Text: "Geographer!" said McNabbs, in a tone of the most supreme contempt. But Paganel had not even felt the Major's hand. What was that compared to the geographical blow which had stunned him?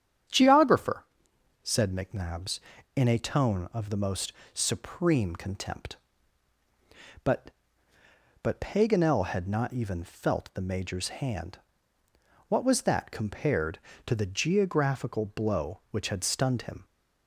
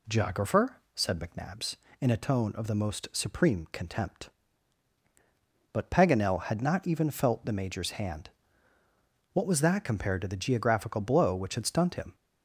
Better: second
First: starts louder than the rest; strong; until 1.8 s; 9 dB // pauses between "most" and "supreme"; slight; at 4.3 s; 0.22 s long // says "But" twice; at 8.4 s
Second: none

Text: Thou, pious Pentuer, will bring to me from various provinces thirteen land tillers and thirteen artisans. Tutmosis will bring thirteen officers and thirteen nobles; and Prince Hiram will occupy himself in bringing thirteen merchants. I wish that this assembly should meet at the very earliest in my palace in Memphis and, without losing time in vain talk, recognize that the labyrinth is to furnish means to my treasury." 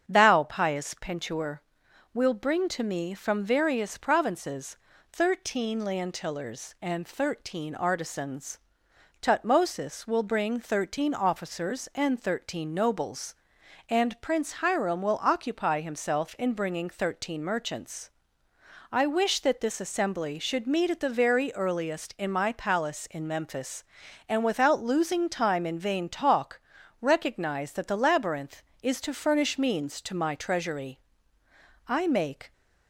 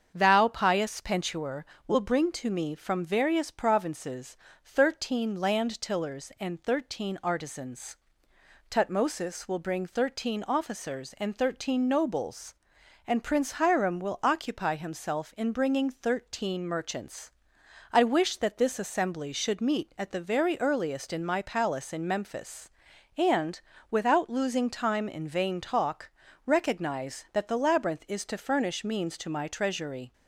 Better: second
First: starts louder than the rest; strong; until 1.0 s; 7.5 dB // pauses between "provinces" and "thirteen"; slight; at 4.7 s; 0.36 s long // goes on to say "I make"; noticeable; from 31.8 s on; 0.64 s long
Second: starts louder than the rest; strong; until 1.1 s; 7.5 dB // pauses between "provinces" and "thirteen"; slight; at 4.3 s; 0.26 s long

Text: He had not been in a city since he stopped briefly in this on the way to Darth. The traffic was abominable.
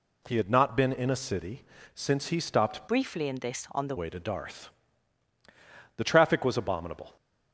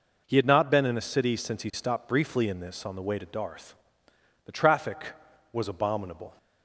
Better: second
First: pauses between "city" and "since"; slight; at 1.6 s; 0.32 s long // changes voice from "briefly" to "the"; from 2.8 to 3.9 s; 1.1 s long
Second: none

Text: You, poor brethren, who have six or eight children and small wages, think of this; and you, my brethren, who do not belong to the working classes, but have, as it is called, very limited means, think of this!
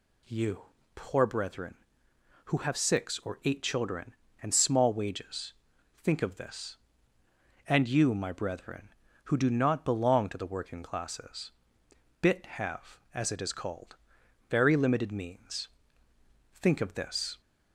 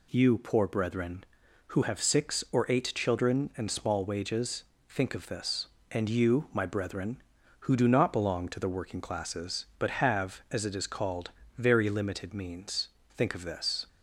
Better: second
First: says "bit" for "but"; at 12.2 s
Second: none

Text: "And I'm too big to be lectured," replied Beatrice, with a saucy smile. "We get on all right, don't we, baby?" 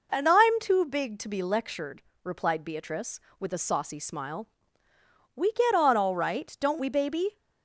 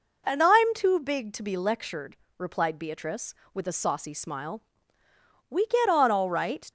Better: first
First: none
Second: stops before "don't we baby"; at 6.6 s

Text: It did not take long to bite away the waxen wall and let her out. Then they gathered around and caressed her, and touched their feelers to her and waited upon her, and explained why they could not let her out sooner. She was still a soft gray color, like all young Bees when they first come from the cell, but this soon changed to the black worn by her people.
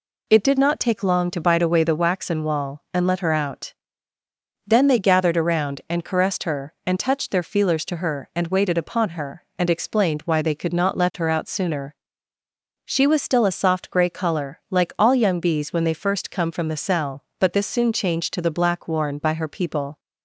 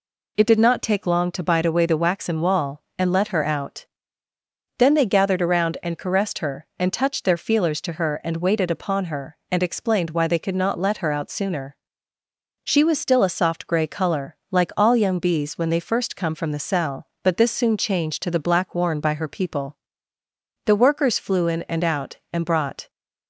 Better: first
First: none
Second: goes on to say "The Workers flew in and out and brought"; strong; from 20.6 s on; 2.2 s long

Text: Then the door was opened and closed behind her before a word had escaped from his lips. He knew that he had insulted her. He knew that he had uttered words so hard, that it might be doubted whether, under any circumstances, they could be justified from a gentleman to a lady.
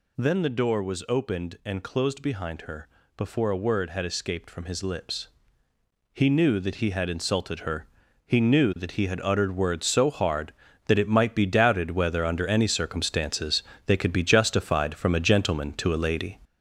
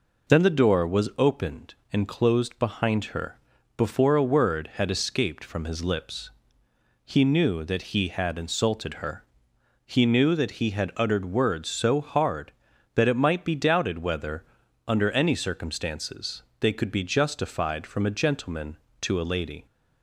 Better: second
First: gets louder; throughout; 6.5 dB // pauses between "her" and "before"; slight; at 2.8 s; 0.30 s long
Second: pauses between "her" and "before"; at 3.3 s; 0.38 s long

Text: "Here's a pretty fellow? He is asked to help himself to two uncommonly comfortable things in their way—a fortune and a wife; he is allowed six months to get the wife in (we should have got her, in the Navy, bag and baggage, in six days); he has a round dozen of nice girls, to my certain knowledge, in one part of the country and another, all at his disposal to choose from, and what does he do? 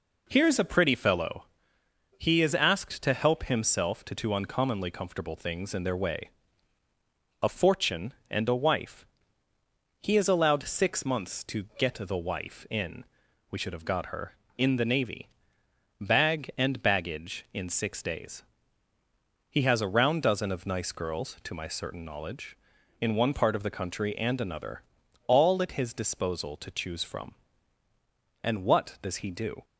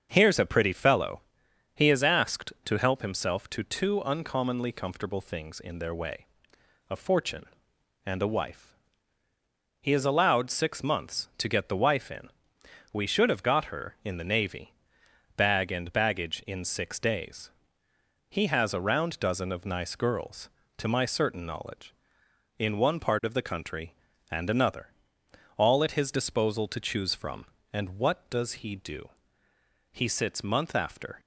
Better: first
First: none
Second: starts louder than the rest; until 1.1 s; 6.5 dB // goes on to say "He sits month after"; noticeable; from 29.9 s on; 1.2 s long

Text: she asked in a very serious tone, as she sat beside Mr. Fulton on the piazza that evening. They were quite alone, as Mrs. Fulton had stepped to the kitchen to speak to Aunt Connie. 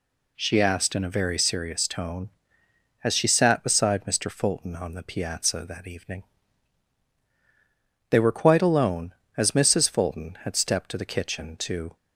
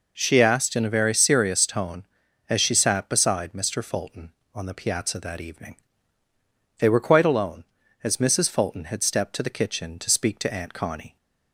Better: second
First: stops before "speak to Aunt Connie"; at 11.9 s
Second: none

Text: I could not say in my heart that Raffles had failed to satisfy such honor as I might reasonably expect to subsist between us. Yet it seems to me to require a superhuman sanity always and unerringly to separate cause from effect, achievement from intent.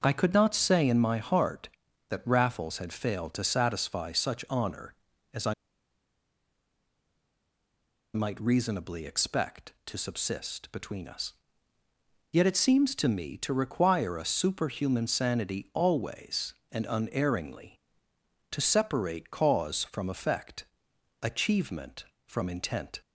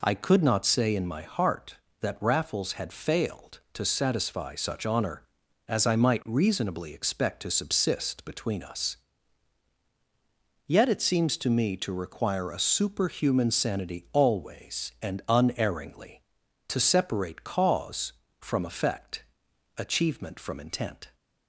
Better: second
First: pauses between "I" and "might"; strong; at 5.5 s; 2.6 s long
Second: none

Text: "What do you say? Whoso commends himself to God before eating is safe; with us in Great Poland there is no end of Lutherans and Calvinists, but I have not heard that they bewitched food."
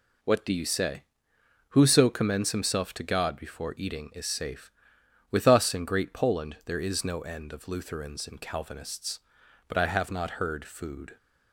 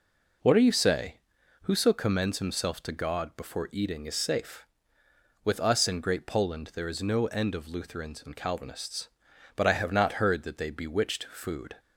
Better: second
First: skips "that they bewitched"; at 10.6 s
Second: none

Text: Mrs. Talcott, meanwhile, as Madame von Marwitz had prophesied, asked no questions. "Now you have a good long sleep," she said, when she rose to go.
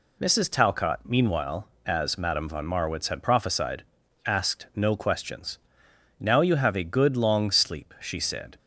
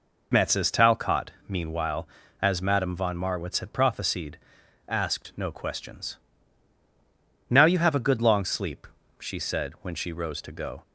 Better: second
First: stops before "when she rose to go"; at 8.5 s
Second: none

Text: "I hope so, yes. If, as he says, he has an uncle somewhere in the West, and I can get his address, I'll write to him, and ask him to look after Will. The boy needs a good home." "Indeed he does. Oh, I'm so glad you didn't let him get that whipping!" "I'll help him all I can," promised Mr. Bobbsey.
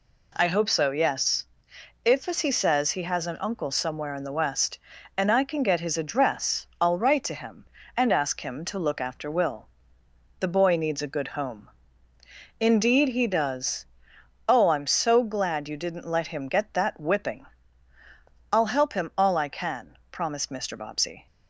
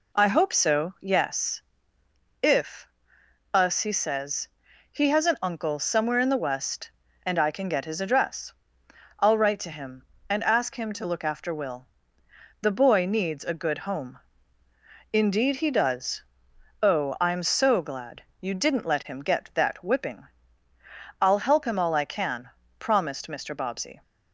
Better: first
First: none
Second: says "us" for "as"; at 3.5 s // pauses between "glad" and "you"; slight; at 18.2 s; 0.18 s long

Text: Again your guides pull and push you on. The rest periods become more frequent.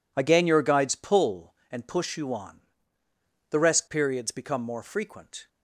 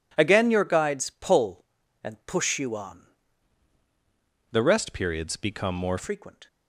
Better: first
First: none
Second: changes voice from "The" to "more"; from 4.5 to 5.9 s; 1.4 s long

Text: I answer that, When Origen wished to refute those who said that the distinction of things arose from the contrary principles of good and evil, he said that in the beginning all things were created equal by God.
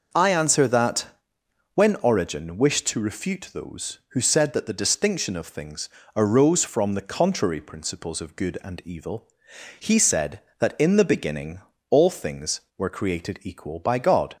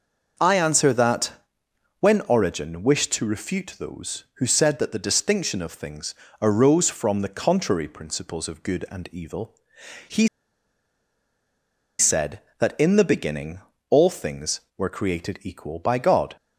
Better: first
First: pauses between "things" and "arose"; slight; at 5.8 s; 0.30 s long // pauses between "beginning" and "all"; slight; at 11.6 s; 0.30 s long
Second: pauses between "things" and "arose"; slight; at 6.1 s; 0.30 s long // pauses between "he" and "said"; strong; at 10.2 s; 1.7 s long // pauses between "beginning" and "all"; slight; at 13.5 s; 0.30 s long

